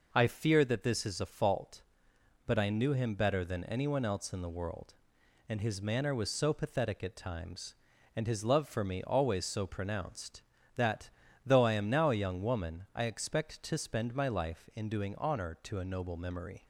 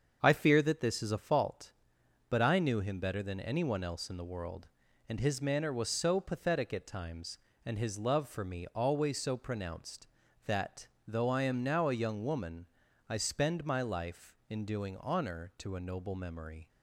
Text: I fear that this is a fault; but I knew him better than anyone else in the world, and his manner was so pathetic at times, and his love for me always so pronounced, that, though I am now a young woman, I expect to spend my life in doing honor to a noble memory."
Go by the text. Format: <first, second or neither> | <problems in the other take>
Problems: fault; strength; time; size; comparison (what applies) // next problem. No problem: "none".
first | starts louder than the rest; until 1.2 s; 7 dB // skips "expect to"; at 13.1 s